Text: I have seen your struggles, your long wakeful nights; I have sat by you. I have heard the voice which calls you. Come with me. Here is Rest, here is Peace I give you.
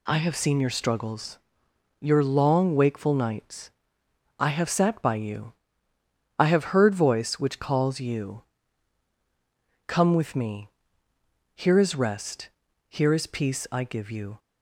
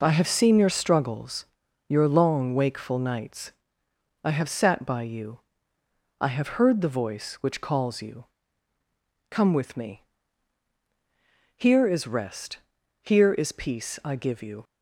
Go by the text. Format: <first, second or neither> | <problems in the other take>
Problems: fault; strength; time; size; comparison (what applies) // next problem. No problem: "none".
second | skips "the"; at 6.9 s